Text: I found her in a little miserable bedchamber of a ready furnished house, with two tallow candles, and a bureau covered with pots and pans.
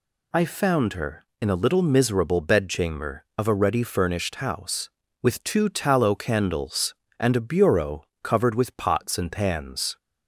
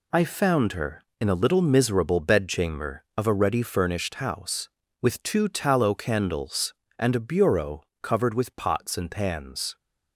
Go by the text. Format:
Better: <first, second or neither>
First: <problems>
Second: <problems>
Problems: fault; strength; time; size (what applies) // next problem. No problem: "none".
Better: first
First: pauses between "bureau" and "covered"; slight; at 8.0 s; 0.18 s long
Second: gets quieter; strong; throughout; 7 dB // pauses between "bureau" and "covered"; slight; at 7.8 s; 0.18 s long